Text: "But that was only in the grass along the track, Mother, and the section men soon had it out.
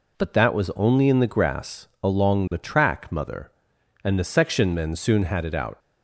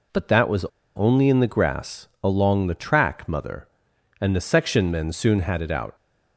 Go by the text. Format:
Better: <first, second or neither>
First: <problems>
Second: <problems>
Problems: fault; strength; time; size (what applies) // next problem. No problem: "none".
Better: first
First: none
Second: pauses between "was" and "only"; slight; at 0.6 s; 0.33 s long